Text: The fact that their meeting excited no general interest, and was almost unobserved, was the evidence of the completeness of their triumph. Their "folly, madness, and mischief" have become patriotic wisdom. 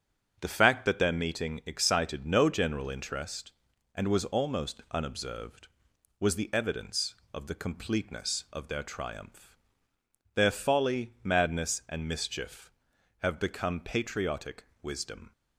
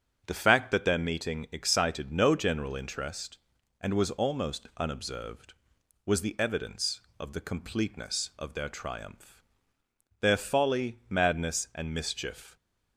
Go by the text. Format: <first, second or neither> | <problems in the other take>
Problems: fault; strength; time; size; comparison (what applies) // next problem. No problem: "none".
first | starts louder than the rest; strong; until 1.2 s; 7.5 dB; strong in the first // stops before "have become patriotic wisdom"; at 12.5 s